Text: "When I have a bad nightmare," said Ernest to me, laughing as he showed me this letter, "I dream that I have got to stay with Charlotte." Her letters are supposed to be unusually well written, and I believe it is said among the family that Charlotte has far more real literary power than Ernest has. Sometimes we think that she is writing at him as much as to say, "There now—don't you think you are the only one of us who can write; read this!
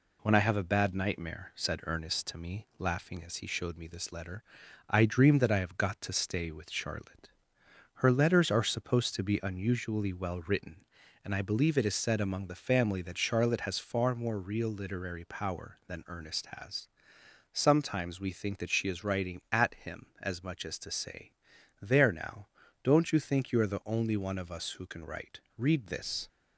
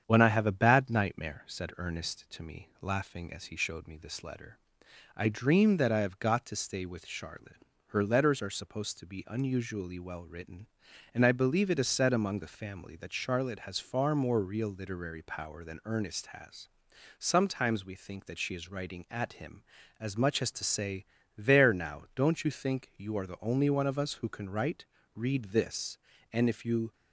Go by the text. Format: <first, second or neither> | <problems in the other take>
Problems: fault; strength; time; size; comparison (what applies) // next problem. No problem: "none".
first | starts louder than the rest; strong; until 1.0 s; 8 dB // goes on to say "And if you"; from 26.3 s on; 0.60 s long